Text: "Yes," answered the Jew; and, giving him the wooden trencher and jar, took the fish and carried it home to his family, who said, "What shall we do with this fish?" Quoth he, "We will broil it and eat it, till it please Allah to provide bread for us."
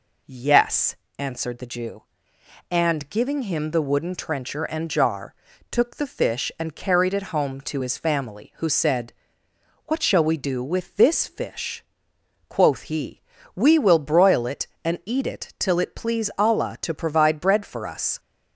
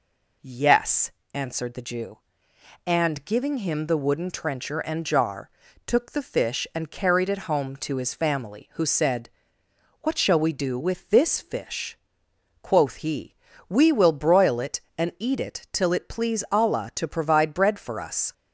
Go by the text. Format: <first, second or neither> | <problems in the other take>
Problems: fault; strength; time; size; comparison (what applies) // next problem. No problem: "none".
neither | none